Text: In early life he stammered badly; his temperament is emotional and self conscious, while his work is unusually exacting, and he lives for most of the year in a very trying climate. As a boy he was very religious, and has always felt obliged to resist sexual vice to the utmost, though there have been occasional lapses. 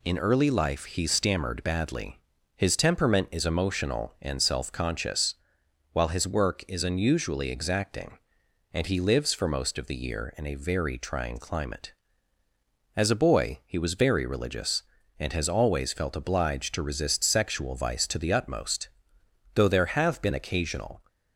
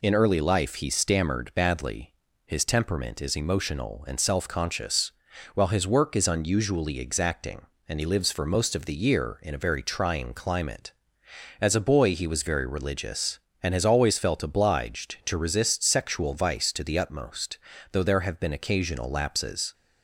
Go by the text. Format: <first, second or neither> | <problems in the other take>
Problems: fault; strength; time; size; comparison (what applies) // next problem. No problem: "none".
second | stops before "lapses"; at 21.0 s